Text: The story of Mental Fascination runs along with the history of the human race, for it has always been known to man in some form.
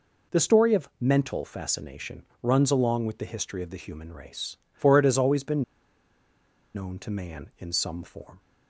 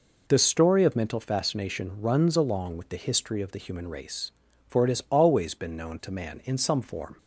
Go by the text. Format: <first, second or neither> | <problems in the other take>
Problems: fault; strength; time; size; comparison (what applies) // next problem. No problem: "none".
second | pauses between "Fascination" and "runs"; slight; at 2.2 s; 0.20 s long // pauses between "been" and "known"; at 5.6 s; 1.1 s long